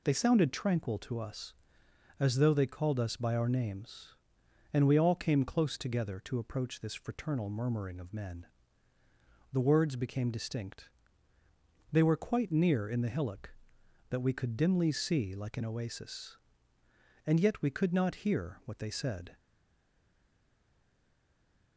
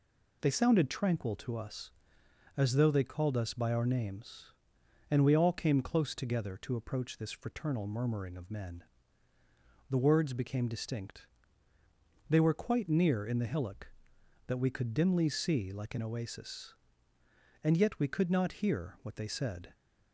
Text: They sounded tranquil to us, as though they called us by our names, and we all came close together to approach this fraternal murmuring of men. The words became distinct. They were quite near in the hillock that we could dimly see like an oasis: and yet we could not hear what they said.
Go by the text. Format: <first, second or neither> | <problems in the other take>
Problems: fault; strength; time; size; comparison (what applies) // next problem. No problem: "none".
second | stays silent after the last word; from 19.3 s on; 2.4 s long